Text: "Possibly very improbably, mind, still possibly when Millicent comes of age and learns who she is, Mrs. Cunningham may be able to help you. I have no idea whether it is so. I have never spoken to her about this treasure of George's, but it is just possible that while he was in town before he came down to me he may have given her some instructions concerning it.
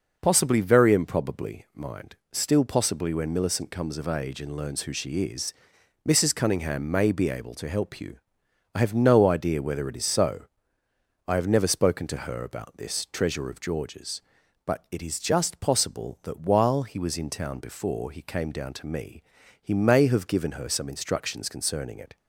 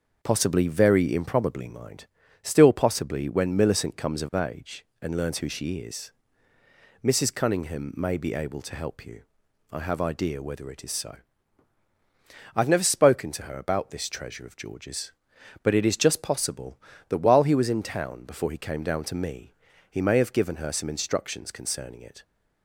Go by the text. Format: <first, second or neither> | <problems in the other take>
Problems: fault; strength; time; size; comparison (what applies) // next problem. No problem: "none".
first | starts louder than the rest; noticeable; until 1.2 s; 6 dB // skips "no"; at 10.0 s // pauses between "me" and "he"; at 19.5 s; 0.38 s long; also in the first